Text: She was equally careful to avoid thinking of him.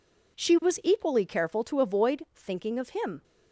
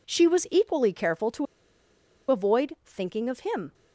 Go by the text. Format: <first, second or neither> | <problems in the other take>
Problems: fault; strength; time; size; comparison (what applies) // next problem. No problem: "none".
first | pauses between "to" and "avoid"; noticeable; at 1.4 s; 0.85 s long